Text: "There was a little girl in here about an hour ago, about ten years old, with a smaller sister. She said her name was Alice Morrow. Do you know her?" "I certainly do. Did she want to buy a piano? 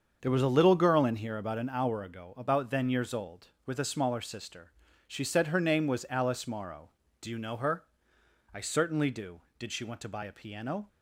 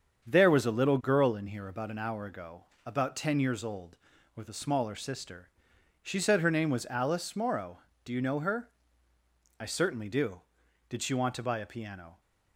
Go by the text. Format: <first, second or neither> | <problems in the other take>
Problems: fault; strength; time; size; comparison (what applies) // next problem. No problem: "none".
second | starts louder than the rest; until 1.2 s; 7 dB; strong in the second // says "then" for "ten"; at 2.6 s